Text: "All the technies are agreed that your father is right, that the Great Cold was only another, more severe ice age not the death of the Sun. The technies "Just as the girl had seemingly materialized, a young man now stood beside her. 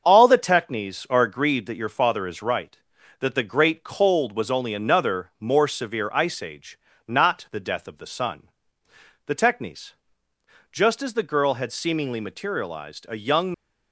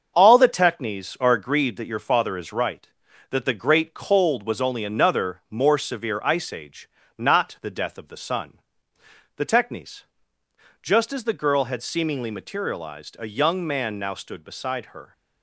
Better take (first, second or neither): second